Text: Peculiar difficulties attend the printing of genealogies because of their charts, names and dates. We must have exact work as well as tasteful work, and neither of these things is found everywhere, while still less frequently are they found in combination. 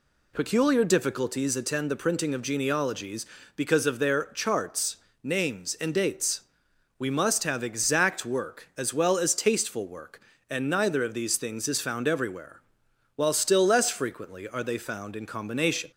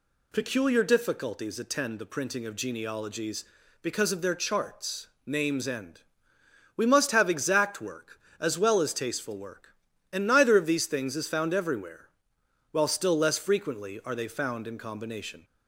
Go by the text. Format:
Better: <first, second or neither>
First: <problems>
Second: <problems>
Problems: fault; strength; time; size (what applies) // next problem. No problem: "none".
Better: first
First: none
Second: skips "dates"; at 6.3 s